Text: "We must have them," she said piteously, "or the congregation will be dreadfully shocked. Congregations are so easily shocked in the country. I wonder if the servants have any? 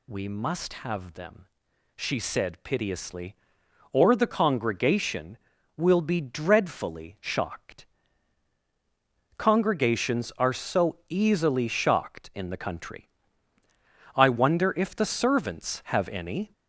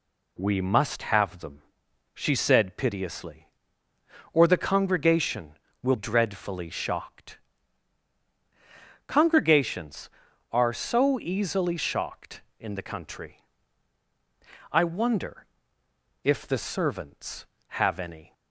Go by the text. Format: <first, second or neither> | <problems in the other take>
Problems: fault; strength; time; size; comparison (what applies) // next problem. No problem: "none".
first | skips "be"; at 5.9 s // pauses between "wonder" and "if"; noticeable; at 15.4 s; 0.78 s long